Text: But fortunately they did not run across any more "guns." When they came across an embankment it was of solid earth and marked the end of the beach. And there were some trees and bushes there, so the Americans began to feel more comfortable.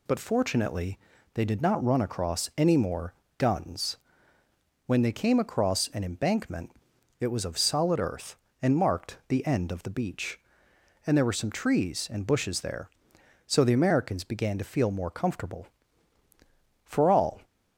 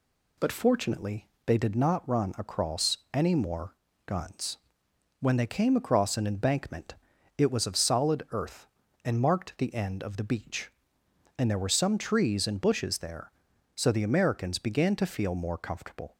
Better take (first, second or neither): second